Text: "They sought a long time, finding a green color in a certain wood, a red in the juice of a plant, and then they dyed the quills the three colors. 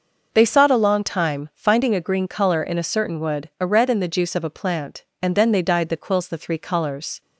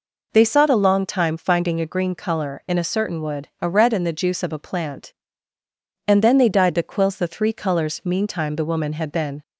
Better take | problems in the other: first | goes on to say "Meantime the woman had been"; from 8.0 s on; 1.3 s long

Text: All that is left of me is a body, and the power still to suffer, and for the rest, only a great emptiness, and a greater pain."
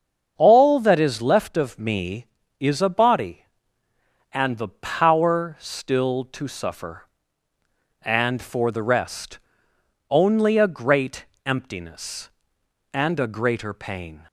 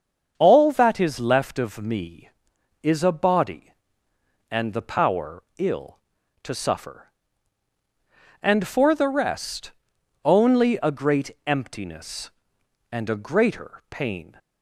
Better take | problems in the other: first | starts louder than the rest; until 1.3 s; 7 dB; also in the first // says "ill" for "still"; at 5.5 s // pauses between "great" and "emptiness"; slight; at 11.3 s; 0.16 s long; slight in the first

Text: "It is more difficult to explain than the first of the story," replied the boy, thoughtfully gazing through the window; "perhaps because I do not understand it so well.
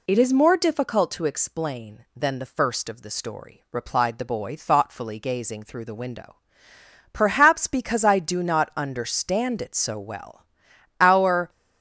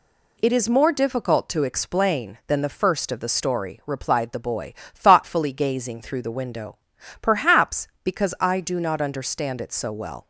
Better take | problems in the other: second | goes on to say "Our"; from 10.9 s on; 0.50 s long

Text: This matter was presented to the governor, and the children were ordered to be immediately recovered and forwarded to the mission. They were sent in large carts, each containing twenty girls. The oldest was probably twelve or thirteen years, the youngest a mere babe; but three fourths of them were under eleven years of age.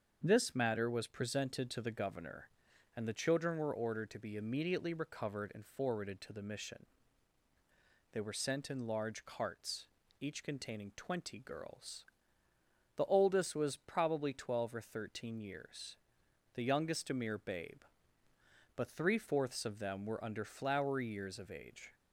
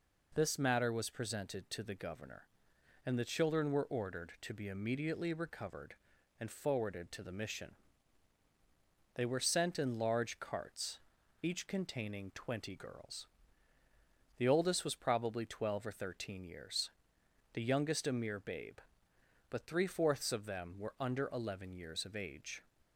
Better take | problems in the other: second | starts louder than the rest; until 1.2 s; 7 dB // says "flowery" for "eleven"; at 20.4 s

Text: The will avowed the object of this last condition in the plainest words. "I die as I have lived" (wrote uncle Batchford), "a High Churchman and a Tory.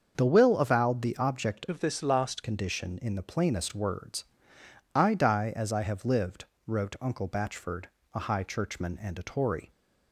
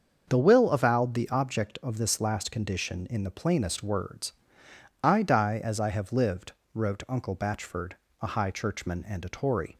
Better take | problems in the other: second | starts louder than the rest; until 1.1 s; 6.5 dB; also in the second // changes voice from "of" to "last"; from 1.6 to 2.4 s; 0.8 s long

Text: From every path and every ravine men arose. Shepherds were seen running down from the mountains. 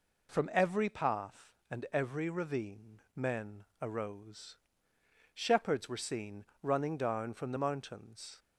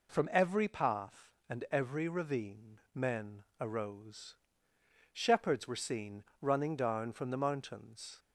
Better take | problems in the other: neither | pauses between "ravine" and "men"; slight; the same in both // pauses between "men" and "arose"; slight; the same in both // pauses between "seen" and "running"; slight; the same in both

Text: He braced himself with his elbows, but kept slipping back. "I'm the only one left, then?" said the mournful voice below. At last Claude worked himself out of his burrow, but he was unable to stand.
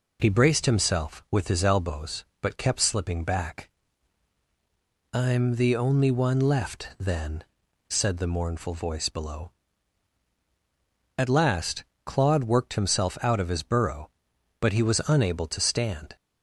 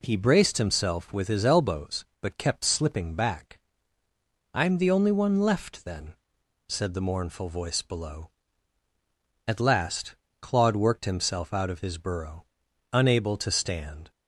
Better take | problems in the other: first | pauses between "last" and "Claude"; slight; at 10.1 s; 0.26 s long; slight in the first // skips "but he was"; at 12.6 s

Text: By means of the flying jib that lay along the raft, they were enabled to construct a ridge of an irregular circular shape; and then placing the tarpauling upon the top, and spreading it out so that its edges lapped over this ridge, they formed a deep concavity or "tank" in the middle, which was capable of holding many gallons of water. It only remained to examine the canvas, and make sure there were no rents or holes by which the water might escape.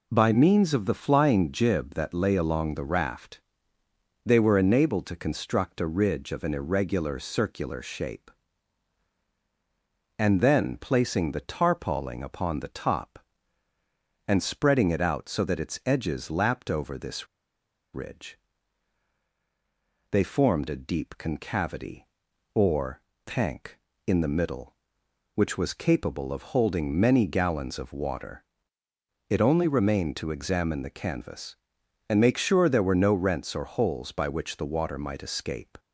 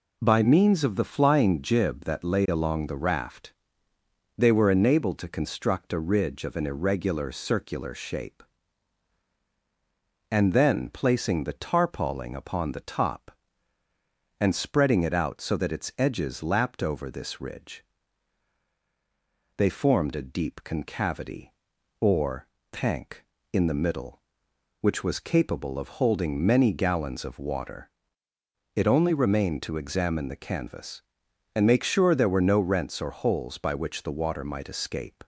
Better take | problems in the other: second | pauses between "this" and "ridge"; noticeable; at 17.2 s; 0.68 s long // pauses between "or" and "tank"; slight; at 22.9 s; 0.26 s long; slight in the second

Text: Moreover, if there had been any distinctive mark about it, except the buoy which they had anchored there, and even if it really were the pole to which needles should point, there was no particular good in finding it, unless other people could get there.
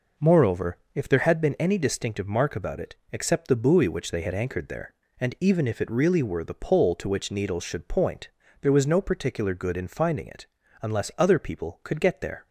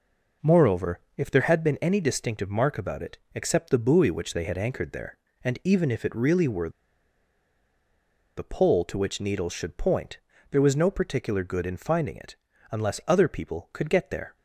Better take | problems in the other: first | pauses between "were" and "the"; strong; at 6.6 s; 1.6 s long

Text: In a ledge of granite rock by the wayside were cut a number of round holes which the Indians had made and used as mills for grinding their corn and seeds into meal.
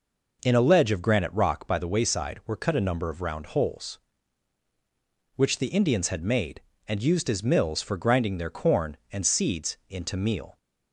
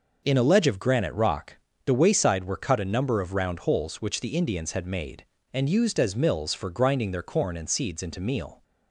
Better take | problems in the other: first | skips "by"; at 1.7 s

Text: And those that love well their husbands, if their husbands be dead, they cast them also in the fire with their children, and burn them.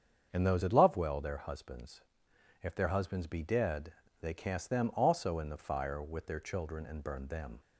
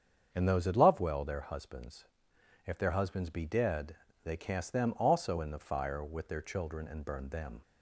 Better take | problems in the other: neither | starts louder than the rest; strong; the same in both

